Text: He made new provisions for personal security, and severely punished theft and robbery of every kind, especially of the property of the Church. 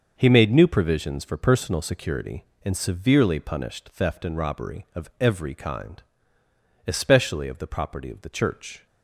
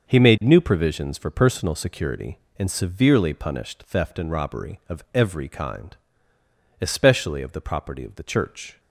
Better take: neither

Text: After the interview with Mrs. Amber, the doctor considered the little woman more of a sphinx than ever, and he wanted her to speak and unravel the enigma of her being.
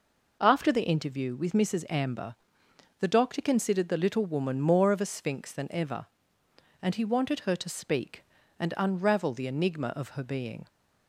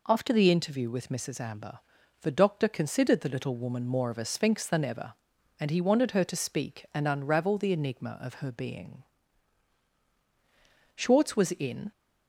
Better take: first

